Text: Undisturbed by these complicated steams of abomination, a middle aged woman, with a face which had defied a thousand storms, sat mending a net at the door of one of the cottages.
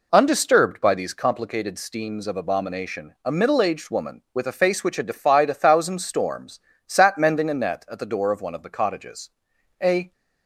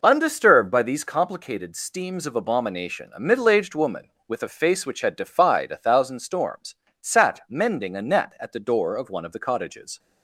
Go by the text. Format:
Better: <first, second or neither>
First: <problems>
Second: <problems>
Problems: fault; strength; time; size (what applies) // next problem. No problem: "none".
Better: second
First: goes on to say "A"; slight; from 9.8 s on; 0.30 s long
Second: none